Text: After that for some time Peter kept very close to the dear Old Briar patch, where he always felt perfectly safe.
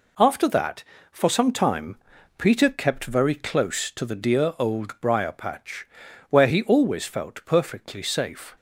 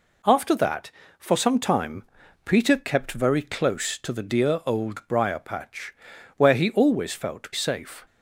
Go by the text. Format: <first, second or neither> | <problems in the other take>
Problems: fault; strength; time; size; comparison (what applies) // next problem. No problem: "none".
first | pauses between "time" and "Peter"; at 2.0 s; 0.42 s long; also in the first // skips "perfectly"; at 7.5 s